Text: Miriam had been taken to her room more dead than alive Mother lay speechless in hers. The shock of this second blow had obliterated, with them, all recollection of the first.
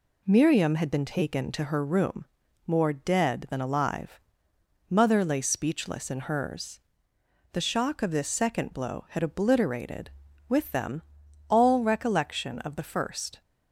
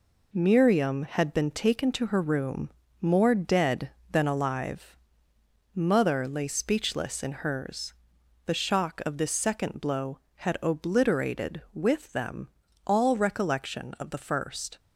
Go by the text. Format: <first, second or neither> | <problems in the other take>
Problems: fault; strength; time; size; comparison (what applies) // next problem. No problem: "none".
first | gets quieter; noticeable; throughout; 6 dB // pauses between "room" and "more"; slight; at 2.7 s; 0.30 s long; also in the first // pauses between "alive" and "Mother"; noticeable; at 4.9 s; 0.76 s long; noticeable in the first